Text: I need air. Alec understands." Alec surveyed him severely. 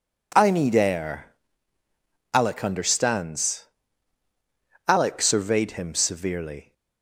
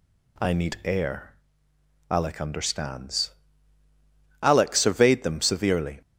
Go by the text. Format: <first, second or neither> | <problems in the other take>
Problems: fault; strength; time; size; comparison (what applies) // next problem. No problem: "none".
first | says "them" for "him"; at 5.2 s